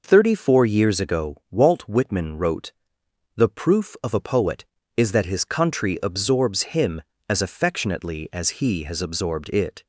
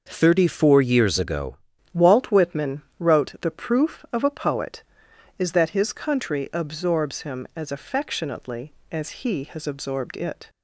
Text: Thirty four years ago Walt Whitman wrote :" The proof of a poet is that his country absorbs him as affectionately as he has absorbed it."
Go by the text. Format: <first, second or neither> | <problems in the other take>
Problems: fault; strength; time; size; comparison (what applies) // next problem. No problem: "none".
first | changes voice at "Walt"; from 1.9 s on; 8.5 s long // pauses between "Whitman" and "wrote"; slight; at 2.8 s; 0.16 s long